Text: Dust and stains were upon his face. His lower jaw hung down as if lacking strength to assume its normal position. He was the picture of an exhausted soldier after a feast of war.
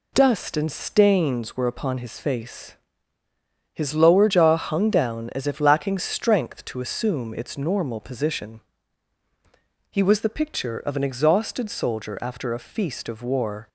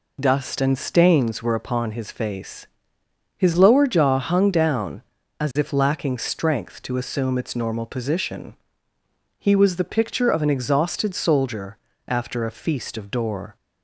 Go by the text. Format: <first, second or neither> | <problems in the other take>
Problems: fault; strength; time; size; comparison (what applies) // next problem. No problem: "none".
first | pauses between "soldier" and "after"; slight; at 11.7 s; 0.28 s long // says "door" for "war"; at 13.0 s